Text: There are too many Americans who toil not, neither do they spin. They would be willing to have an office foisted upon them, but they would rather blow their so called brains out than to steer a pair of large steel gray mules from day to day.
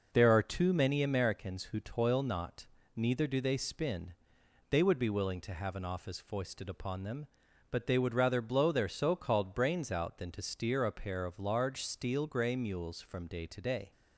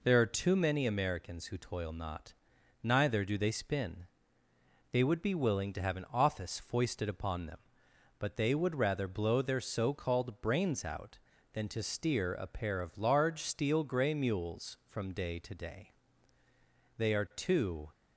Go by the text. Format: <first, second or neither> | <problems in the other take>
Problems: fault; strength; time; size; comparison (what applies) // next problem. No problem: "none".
first | goes on to say "They are too"; noticeable; from 16.9 s on; 0.93 s long